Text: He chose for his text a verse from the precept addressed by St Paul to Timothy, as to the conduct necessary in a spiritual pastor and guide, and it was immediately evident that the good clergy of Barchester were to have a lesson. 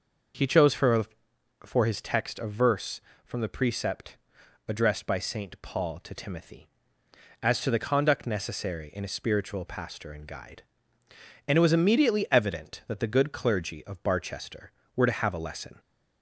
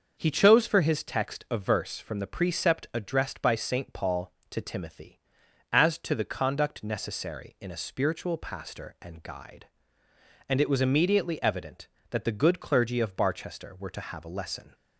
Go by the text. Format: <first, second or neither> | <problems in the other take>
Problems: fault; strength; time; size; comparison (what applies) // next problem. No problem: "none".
second | starts louder than the rest; noticeable; until 1.9 s; 6 dB; also in the second // says "for" twice; at 1.6 s // pauses between "precept" and "addressed"; noticeable; at 4.1 s; 0.50 s long